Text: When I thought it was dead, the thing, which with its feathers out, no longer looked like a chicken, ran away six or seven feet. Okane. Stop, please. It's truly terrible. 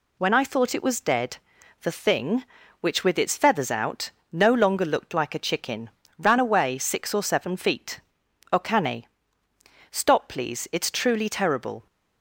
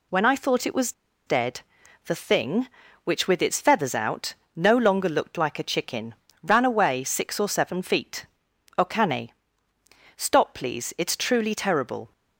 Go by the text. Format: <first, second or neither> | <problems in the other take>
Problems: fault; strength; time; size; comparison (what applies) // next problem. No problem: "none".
first | pauses between "was" and "dead"; slight; at 0.9 s; 0.34 s long